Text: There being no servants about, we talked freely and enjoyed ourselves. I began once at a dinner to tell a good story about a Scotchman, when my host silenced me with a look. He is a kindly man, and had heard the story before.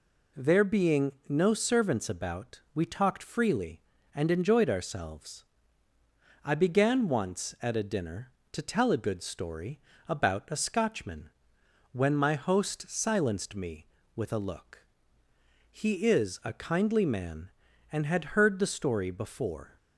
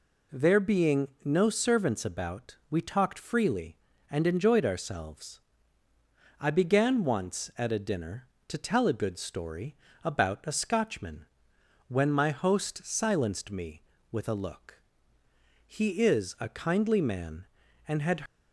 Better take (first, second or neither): first